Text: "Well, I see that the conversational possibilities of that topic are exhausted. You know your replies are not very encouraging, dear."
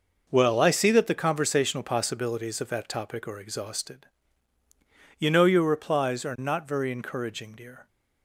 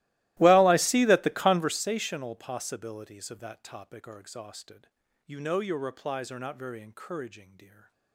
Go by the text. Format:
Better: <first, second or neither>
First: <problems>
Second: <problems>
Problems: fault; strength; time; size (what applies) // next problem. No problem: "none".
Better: first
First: none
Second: starts louder than the rest; strong; until 1.8 s; 17 dB